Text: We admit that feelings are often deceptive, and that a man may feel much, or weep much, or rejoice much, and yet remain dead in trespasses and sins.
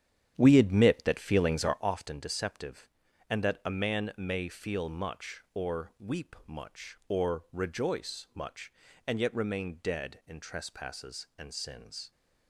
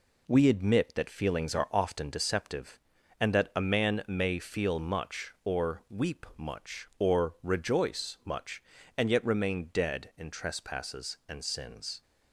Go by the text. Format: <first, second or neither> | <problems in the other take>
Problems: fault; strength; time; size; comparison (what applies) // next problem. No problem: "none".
second | starts louder than the rest; strong; until 1.9 s; 9.5 dB